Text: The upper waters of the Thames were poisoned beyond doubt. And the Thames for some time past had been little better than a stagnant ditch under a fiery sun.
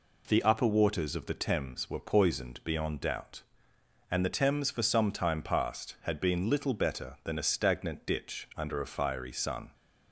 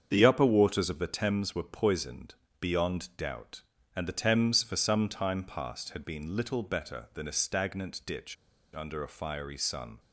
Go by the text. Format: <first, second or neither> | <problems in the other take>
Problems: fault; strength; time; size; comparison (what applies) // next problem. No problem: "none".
first | starts louder than the rest; strong; until 1.1 s; 7.5 dB // pauses between "poisoned" and "beyond"; slight; at 2.3 s; 0.26 s long // pauses between "ditch" and "under"; at 8.3 s; 0.38 s long